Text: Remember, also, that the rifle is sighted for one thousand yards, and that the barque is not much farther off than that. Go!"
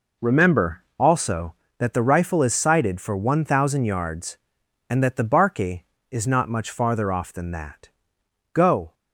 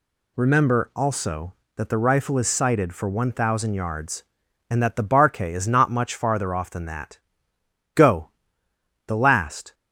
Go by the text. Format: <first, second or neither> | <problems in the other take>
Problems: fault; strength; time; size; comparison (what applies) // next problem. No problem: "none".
first | goes on to say "The last"; noticeable; from 9.0 s on; 0.68 s long